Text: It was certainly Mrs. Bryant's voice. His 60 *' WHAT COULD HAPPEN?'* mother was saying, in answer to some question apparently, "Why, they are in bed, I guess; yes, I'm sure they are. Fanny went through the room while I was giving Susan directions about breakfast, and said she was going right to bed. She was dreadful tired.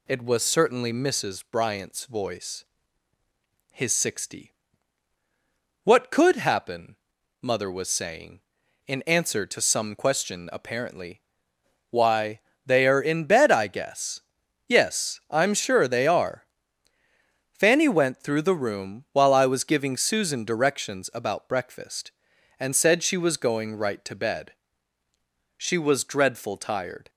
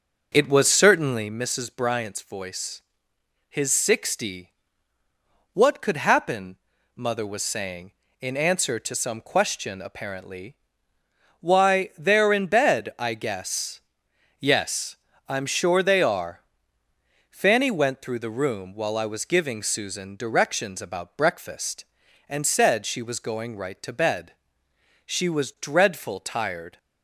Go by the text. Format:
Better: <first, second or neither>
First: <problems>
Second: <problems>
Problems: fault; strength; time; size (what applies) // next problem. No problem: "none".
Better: first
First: none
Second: starts louder than the rest; until 1.4 s; 6.5 dB